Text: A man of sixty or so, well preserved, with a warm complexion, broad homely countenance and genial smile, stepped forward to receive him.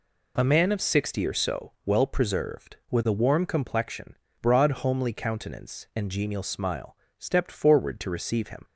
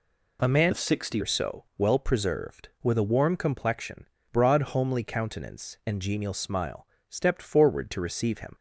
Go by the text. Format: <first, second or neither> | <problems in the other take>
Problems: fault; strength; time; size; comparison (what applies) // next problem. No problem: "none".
first | changes voice from "of" to "sixty"; from 0.7 to 1.1 s; 0.4 s long